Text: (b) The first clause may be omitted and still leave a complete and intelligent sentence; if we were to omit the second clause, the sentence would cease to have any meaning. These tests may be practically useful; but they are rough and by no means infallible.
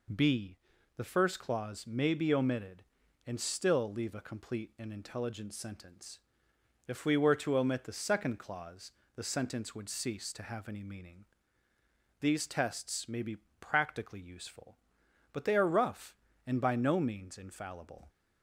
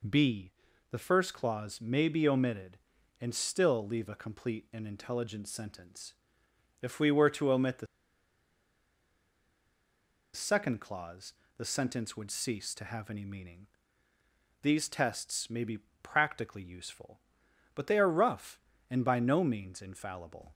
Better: first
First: pauses between "be" and "practically"; slight; at 13.3 s; 0.23 s long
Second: pauses between "the" and "second"; strong; at 7.8 s; 2.4 s long // pauses between "be" and "practically"; slight; at 15.7 s; 0.24 s long

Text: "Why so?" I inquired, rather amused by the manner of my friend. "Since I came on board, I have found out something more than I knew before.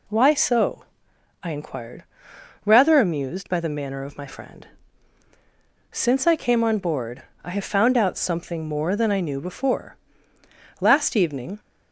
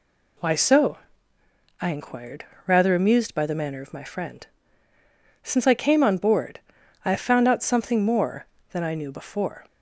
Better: second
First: goes on to say "Last evening"; noticeable; from 10.7 s on; 0.80 s long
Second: none

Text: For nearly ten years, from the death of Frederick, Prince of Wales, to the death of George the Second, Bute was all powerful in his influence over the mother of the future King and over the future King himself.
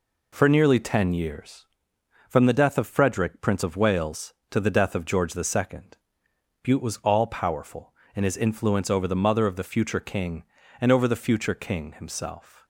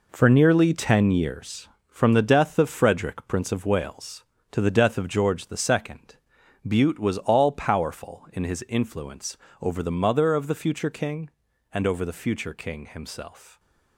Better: first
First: none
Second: gets quieter; strong; throughout; 8.5 dB // pauses between "influence" and "over"; slight; at 9.3 s; 0.26 s long

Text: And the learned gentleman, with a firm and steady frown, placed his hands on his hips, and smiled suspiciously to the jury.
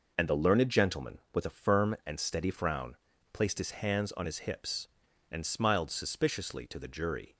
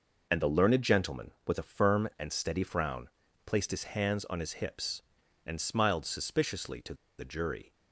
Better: first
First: none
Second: pauses between "to" and "the"; slight; at 6.9 s; 0.24 s long

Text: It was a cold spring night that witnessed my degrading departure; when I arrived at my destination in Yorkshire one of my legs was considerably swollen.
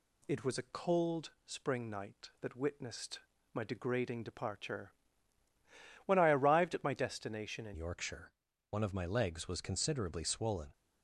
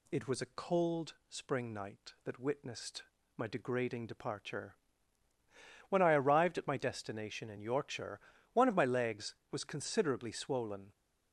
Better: second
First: pauses between "witnessed" and "my"; slight; at 3.1 s; 0.34 s long // changes voice at "Yorkshire"; from 7.7 s on; 3.0 s long // pauses between "Yorkshire" and "one"; at 8.3 s; 0.38 s long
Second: pauses between "witnessed" and "my"; slight; at 3.0 s; 0.34 s long // pauses between "Yorkshire" and "one"; slight; at 8.1 s; 0.34 s long

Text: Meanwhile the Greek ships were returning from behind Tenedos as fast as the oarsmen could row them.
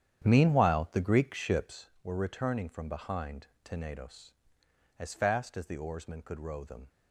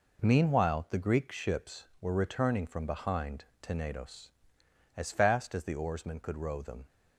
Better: second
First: starts louder than the rest; strong; until 1.8 s; 9.5 dB // pauses between "behind" and "Tenedos"; slight; at 3.4 s; 0.18 s long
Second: pauses between "behind" and "Tenedos"; slight; at 3.4 s; 0.18 s long

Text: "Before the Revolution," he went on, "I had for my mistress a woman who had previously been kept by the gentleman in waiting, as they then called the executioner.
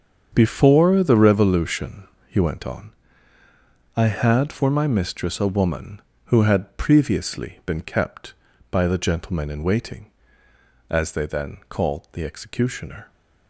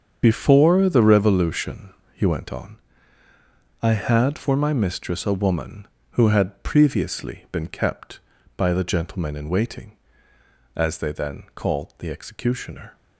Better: first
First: starts louder than the rest; until 1.3 s; 7 dB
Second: loses the start of "Before"; at 0.2 s; 50 ms // starts louder than the rest; until 1.2 s; 7 dB

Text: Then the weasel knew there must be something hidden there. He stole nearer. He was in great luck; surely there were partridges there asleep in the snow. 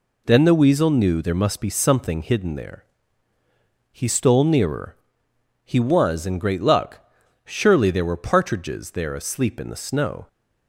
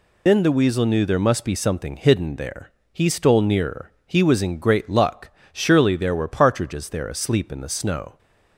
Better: first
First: none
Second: loses the start of "Then"; at 0.2 s; 110 ms

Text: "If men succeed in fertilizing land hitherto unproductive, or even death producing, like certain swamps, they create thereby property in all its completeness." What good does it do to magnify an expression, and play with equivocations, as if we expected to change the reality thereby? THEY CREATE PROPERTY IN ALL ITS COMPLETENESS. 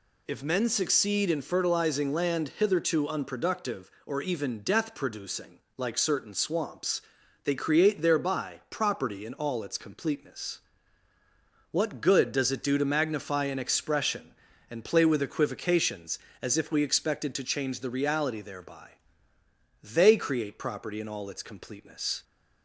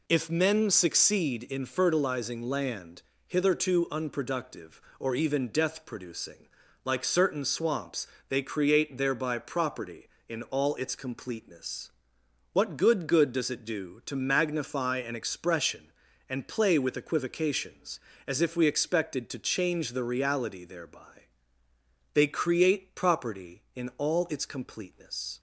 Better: first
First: none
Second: pauses between "land" and "hitherto"; slight; at 3.0 s; 0.26 s long // says "good" twice; at 13.0 s

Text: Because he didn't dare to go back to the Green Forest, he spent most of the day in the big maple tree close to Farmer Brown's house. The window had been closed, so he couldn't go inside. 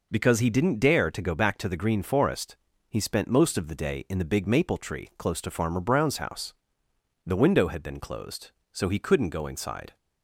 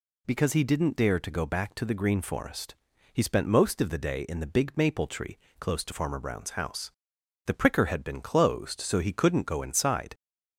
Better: first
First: none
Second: pauses between "tree" and "close"; slight; at 5.3 s; 0.22 s long // says "pricker" for "window"; at 7.5 s

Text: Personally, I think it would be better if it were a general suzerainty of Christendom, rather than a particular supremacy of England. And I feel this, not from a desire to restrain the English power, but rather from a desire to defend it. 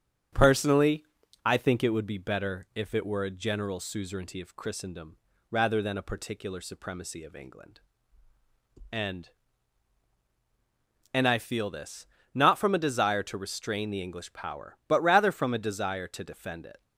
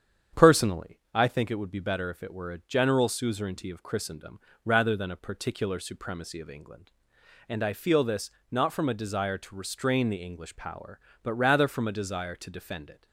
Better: second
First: starts louder than the rest; strong; until 1.7 s; 9 dB // says "And" twice; at 11.1 s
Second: starts louder than the rest; strong; until 1.5 s; 8.5 dB

